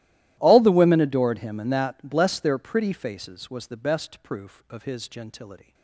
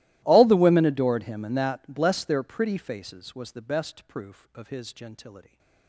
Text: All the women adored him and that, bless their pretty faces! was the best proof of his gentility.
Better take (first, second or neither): first